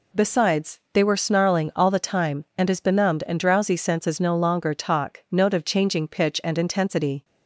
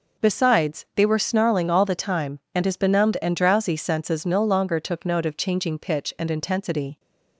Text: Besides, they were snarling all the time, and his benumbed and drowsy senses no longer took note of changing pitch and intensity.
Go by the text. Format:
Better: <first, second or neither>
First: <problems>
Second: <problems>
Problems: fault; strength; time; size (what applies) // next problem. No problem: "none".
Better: second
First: says "talk" for "took"; at 4.7 s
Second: none